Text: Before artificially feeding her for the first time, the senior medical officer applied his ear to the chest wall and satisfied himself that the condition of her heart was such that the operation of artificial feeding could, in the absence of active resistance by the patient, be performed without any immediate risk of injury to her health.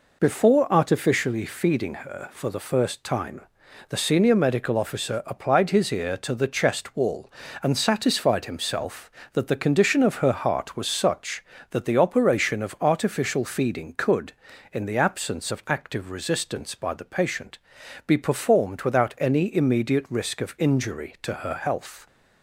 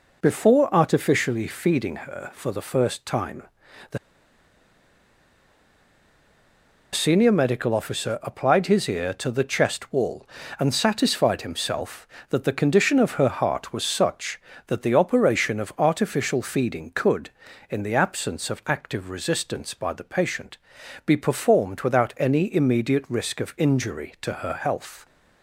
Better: first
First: none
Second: pauses between "the" and "senior"; strong; at 3.9 s; 2.9 s long

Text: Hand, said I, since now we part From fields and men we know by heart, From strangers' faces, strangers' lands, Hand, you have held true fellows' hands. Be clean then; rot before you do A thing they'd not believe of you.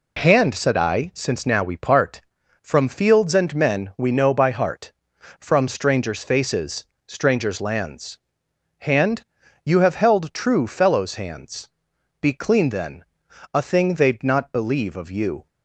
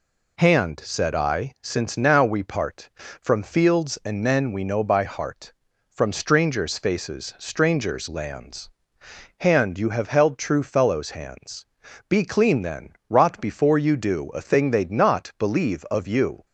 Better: second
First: skips "rot before you do"; at 13.2 s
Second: none

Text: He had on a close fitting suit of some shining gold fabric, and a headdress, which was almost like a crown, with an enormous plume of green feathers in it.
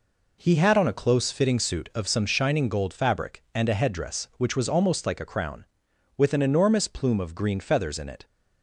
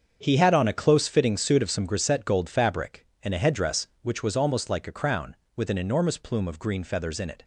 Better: first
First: none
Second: starts louder than the rest; strong; until 1.2 s; 7 dB // says "grisette" for "shining"; at 1.8 s

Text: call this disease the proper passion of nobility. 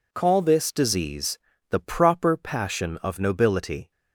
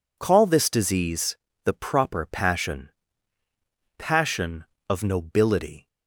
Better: first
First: pauses between "disease" and "the"; slight; at 1.3 s; 0.32 s long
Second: pauses between "disease" and "the"; slight; at 1.3 s; 0.30 s long // says "passion" twice; at 3.9 s

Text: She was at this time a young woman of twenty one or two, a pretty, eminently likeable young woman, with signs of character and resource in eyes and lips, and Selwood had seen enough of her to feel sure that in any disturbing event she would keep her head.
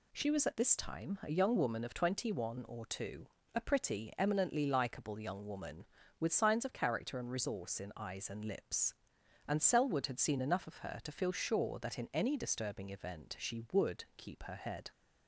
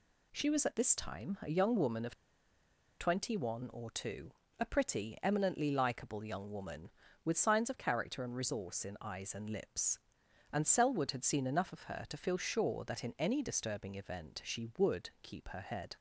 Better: first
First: none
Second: pauses between "of" and "twenty"; noticeable; at 2.1 s; 0.85 s long

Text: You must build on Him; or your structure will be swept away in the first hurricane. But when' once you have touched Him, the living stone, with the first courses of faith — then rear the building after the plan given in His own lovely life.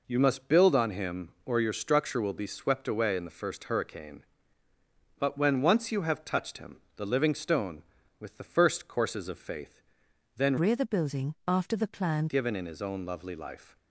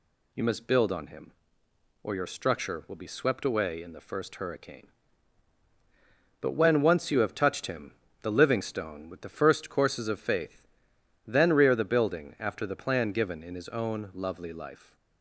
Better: second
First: changes voice from "rear" to "plan"; from 10.5 to 12.2 s; 1.7 s long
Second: none

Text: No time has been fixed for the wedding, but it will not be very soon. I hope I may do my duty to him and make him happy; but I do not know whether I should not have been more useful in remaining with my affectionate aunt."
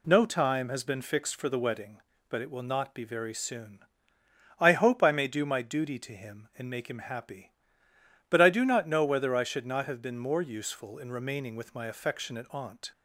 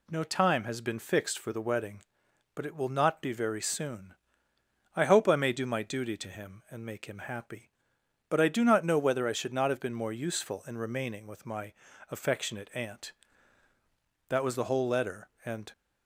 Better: first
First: none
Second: pauses between "my" and "affectionate"; at 11.7 s; 0.40 s long // goes on to say "That was the whole letter and"; from 14.2 s on; 1.4 s long

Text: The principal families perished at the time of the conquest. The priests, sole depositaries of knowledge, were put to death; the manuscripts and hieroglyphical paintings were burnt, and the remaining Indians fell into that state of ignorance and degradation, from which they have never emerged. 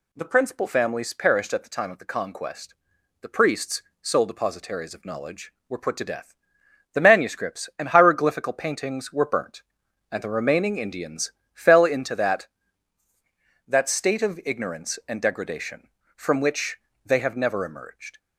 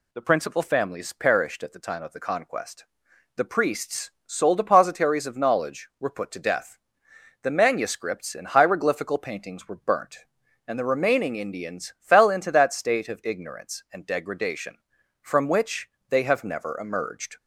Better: second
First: pauses between "Indians" and "fell"; slight; at 11.3 s; 0.22 s long // says "that" twice; at 13.6 s // pauses between "which" and "they"; slight; at 16.7 s; 0.30 s long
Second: pauses between "which" and "they"; slight; at 15.8 s; 0.20 s long

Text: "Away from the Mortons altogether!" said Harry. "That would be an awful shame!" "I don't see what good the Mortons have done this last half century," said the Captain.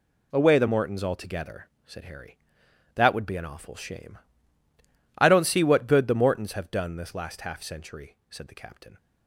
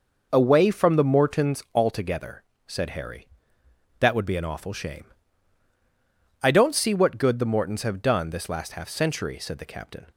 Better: second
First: skips "from"; at 0.5 s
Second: none

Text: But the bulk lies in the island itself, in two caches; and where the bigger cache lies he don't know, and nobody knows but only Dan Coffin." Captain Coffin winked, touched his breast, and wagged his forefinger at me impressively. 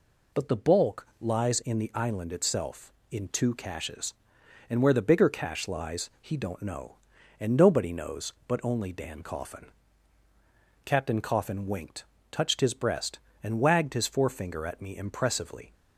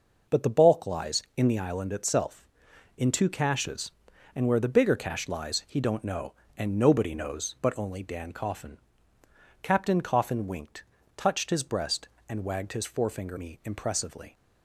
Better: first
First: none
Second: skips "at"; at 13.3 s

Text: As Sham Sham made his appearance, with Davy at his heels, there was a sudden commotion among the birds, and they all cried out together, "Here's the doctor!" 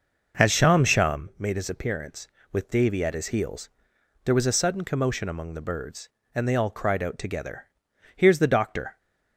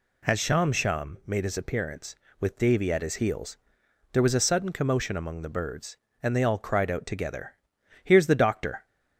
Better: second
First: starts louder than the rest; noticeable; until 1.3 s; 5.5 dB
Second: none

